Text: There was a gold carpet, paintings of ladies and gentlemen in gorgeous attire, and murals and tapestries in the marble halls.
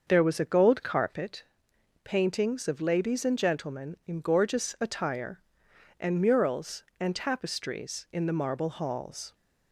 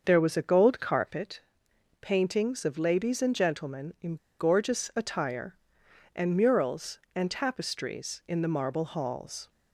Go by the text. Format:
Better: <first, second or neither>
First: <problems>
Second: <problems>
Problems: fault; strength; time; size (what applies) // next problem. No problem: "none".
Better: first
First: starts louder than the rest; until 1.0 s; 6.5 dB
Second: starts louder than the rest; until 1.0 s; 6.5 dB // pauses between "in" and "gorgeous"; slight; at 4.1 s; 0.22 s long